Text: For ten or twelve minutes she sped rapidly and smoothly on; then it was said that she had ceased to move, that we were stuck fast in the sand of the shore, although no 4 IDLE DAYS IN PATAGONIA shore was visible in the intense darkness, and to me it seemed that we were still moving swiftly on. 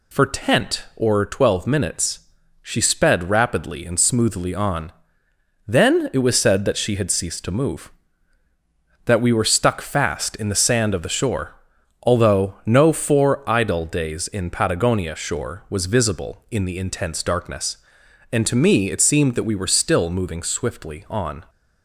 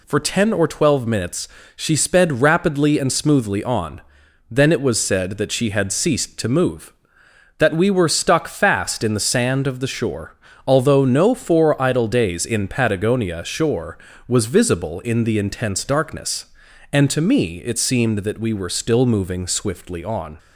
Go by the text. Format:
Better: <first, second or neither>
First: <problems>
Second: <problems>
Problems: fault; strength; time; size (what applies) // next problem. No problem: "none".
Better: second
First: says "tent" for "ten"; at 0.2 s // pauses between "minutes" and "she"; at 2.1 s; 0.42 s long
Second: pauses between "minutes" and "she"; slight; at 1.4 s; 0.26 s long